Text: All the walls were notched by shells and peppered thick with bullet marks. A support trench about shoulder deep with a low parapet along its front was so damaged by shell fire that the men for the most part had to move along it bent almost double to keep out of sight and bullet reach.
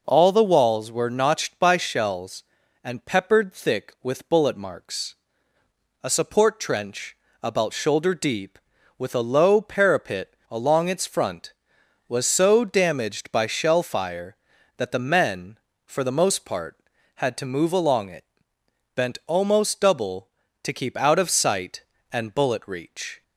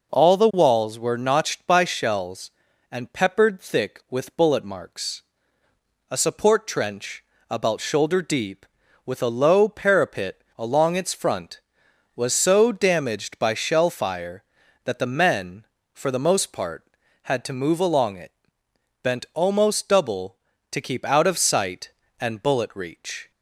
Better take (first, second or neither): neither